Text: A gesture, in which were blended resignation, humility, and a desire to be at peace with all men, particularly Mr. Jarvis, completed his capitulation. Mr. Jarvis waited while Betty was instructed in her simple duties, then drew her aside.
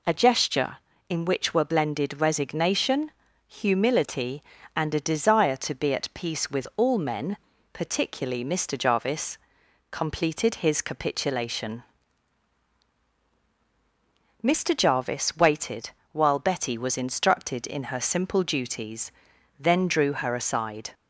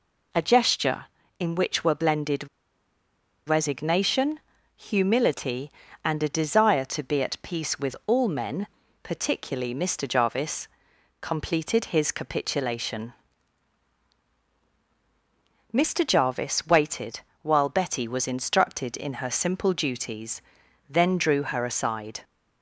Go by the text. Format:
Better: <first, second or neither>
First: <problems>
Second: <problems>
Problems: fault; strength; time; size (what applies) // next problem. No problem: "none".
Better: first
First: pauses between "waited" and "while"; slight; at 15.8 s; 0.24 s long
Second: pauses between "blended" and "resignation"; at 2.4 s; 1.0 s long // pauses between "waited" and "while"; slight; at 17.1 s; 0.24 s long